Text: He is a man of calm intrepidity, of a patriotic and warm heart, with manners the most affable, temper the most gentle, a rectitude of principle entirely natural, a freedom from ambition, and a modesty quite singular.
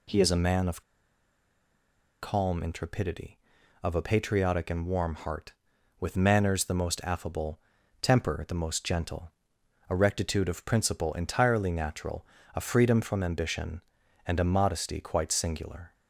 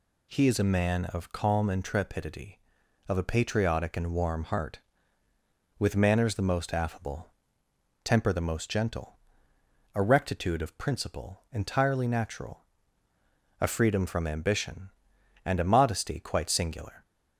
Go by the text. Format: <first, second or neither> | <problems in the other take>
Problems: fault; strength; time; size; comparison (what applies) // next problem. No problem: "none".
second | pauses between "of" and "calm"; strong; at 0.8 s; 1.4 s long